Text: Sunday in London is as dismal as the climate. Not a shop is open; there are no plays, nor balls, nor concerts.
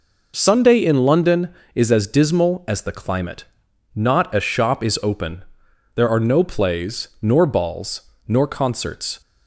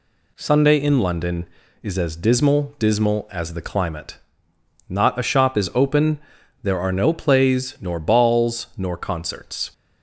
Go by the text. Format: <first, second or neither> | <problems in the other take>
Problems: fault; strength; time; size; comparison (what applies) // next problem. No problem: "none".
first | says "dismal" twice; at 2.7 s